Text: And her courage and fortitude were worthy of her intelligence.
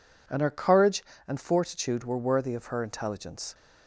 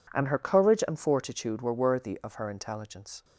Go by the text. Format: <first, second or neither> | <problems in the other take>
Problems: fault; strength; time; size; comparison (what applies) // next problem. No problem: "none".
neither | none